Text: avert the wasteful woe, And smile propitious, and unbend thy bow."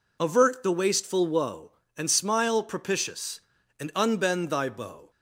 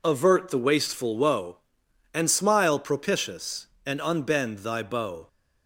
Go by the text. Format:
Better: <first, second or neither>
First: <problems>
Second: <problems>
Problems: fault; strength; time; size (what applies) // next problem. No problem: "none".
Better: neither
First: none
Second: none